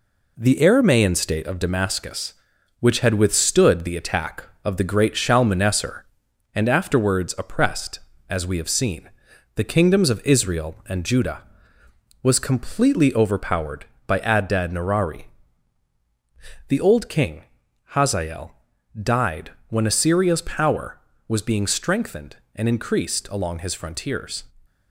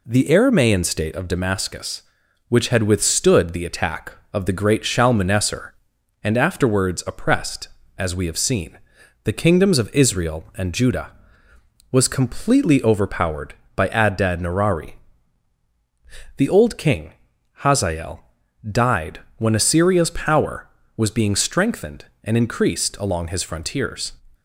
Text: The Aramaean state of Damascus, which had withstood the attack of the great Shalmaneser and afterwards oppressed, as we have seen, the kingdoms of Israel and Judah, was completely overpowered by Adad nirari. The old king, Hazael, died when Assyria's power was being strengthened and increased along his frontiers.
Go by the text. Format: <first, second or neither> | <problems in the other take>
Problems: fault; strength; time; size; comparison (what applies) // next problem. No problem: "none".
second | gets quieter; noticeable; throughout; 4.5 dB // pauses between "died" and "when"; slight; at 19.5 s; 0.18 s long; slight in the second